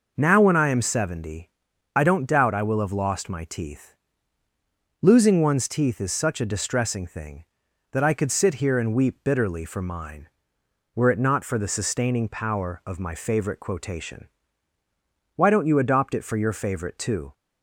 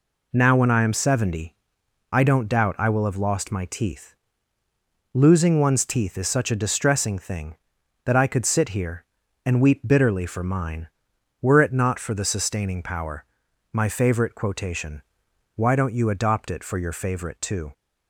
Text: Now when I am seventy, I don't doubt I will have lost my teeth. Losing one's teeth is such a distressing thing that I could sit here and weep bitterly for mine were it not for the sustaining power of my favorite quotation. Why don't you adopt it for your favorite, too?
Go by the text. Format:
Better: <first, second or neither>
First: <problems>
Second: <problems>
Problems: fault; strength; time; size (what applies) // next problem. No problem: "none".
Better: first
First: none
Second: skips "of"; at 13.4 s